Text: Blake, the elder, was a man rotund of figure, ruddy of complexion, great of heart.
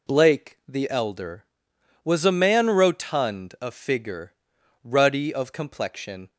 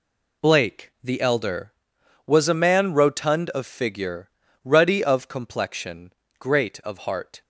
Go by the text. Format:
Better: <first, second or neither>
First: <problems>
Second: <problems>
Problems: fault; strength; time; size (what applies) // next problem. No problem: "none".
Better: second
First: stops before "great of heart"; at 6.2 s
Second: none